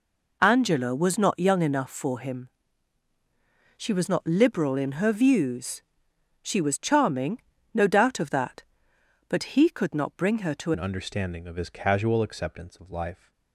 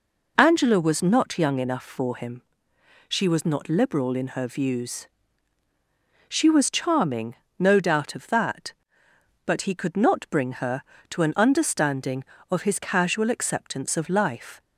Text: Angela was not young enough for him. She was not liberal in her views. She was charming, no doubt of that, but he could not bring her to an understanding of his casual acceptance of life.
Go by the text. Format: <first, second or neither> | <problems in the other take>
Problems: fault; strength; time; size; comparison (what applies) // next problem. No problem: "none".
second | changes voice at "an"; from 10.7 s on; 2.6 s long